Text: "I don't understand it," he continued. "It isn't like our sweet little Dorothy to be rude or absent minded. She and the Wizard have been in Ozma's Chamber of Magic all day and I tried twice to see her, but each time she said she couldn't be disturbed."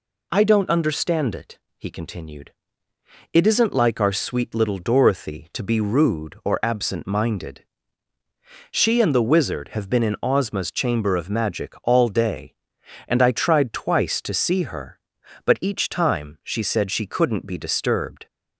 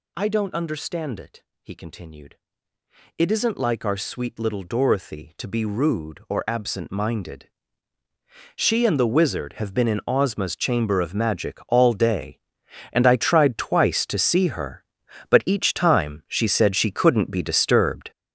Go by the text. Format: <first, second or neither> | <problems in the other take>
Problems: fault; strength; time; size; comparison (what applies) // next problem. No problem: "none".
first | gets louder; strong; throughout; 9 dB